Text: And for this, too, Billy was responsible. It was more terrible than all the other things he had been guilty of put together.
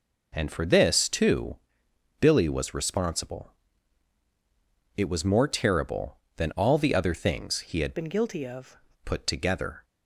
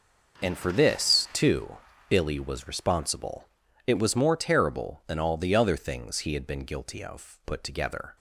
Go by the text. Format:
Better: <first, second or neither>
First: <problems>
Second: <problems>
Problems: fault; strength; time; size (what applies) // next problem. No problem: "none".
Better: second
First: changes voice from "been" to "of"; from 7.9 to 8.7 s; 0.8 s long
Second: none